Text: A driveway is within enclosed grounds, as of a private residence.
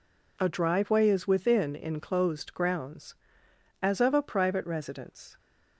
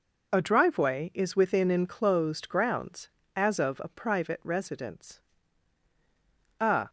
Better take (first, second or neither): first